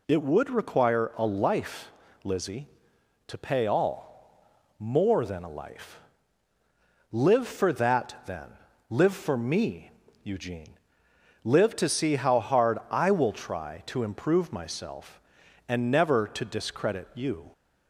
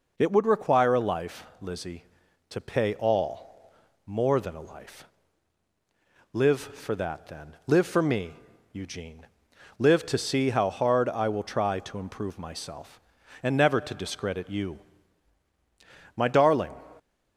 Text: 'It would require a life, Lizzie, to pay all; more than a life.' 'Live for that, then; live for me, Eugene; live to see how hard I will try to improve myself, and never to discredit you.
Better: first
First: none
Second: goes on to say "My darling"; from 16.1 s on; 0.56 s long

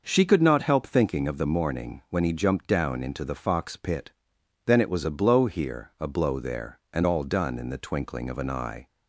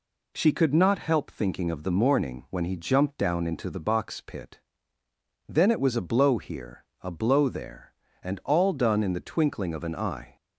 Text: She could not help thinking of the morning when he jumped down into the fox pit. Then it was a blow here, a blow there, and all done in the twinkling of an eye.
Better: first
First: none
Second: says "box" for "fox"; at 3.7 s

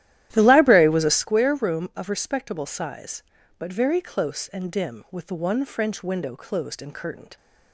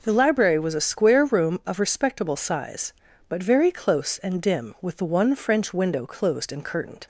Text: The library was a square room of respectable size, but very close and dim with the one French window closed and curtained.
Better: second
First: starts louder than the rest; strong; until 1.3 s; 12.5 dB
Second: none

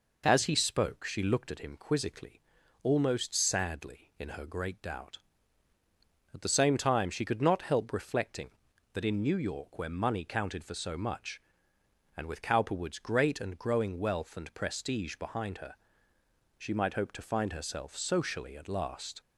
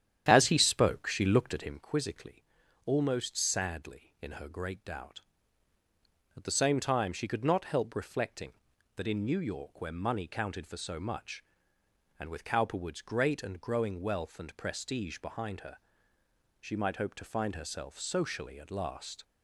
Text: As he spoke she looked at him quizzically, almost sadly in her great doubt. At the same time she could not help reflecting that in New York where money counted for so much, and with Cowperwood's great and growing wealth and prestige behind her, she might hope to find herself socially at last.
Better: first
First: none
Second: starts louder than the rest; strong; until 1.8 s; 10 dB

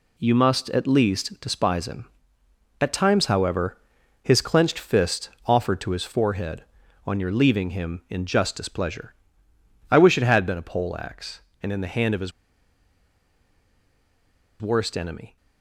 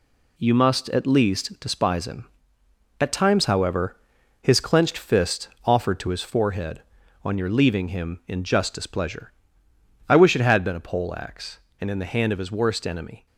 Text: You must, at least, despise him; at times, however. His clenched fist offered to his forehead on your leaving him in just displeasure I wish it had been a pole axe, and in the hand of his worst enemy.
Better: second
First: pauses between "fist" and "offered"; slight; at 5.2 s; 0.16 s long // pauses between "displeasure" and "I"; noticeable; at 9.1 s; 0.76 s long // pauses between "his" and "worst"; strong; at 12.3 s; 2.3 s long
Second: pauses between "fist" and "offered"; slight; at 5.4 s; 0.16 s long // pauses between "displeasure" and "I"; noticeable; at 9.3 s; 0.76 s long

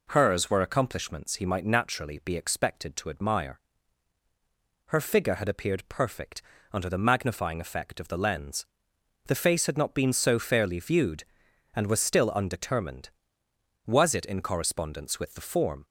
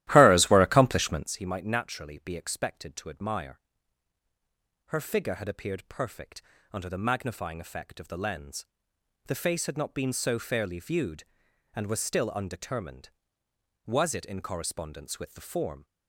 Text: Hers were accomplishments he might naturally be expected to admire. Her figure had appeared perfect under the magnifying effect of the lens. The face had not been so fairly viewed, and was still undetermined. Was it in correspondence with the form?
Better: first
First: pauses between "perfect" and "under"; slight; at 6.4 s; 0.32 s long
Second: starts louder than the rest; strong; until 1.3 s; 14.5 dB // pauses between "perfect" and "under"; slight; at 6.4 s; 0.32 s long

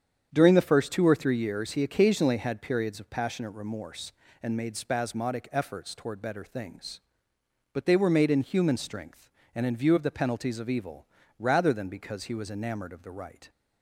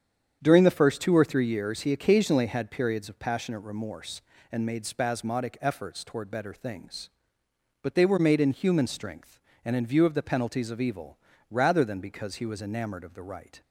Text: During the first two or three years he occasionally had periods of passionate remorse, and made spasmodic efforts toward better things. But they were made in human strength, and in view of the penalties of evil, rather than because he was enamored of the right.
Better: neither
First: starts louder than the rest; strong; until 1.3 s; 8 dB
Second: starts louder than the rest; strong; until 1.4 s; 8 dB

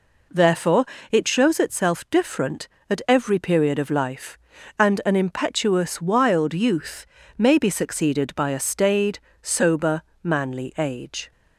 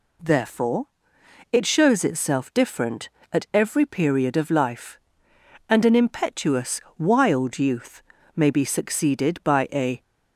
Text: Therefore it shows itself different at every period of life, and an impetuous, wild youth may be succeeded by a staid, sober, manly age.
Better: first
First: pauses between "Therefore" and "it"; slight; at 0.8 s; 0.26 s long // pauses between "youth" and "may"; slight; at 7.0 s; 0.30 s long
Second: pauses between "Therefore" and "it"; noticeable; at 0.8 s; 0.68 s long // pauses between "youth" and "may"; slight; at 8.0 s; 0.34 s long // stops before "staid sober manly age"; at 10.0 s

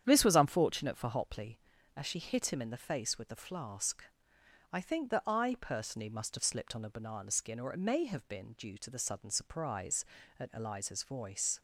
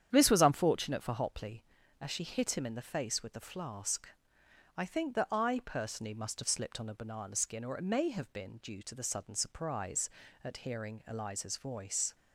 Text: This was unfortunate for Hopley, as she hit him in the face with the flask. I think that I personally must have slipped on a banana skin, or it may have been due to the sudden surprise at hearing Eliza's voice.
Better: second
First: starts louder than the rest; strong; until 1.0 s; 9 dB // skips "hearing"; at 10.5 s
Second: starts louder than the rest; strong; until 1.1 s; 9 dB

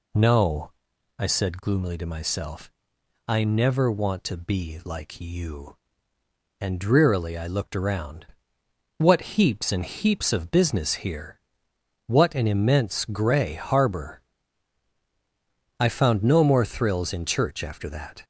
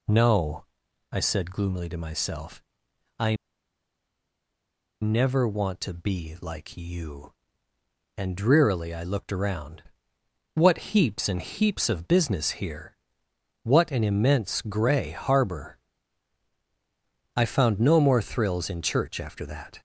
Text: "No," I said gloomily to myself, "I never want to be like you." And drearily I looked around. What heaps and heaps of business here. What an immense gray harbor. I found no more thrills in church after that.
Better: first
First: none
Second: pauses between "I" and "never"; strong; at 3.3 s; 1.6 s long

